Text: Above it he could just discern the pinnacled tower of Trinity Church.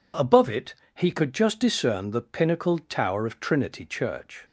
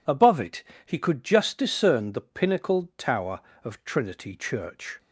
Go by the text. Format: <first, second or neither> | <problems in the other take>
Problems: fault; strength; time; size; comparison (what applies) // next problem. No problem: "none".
neither | pauses between "it" and "he"; slight; the same in both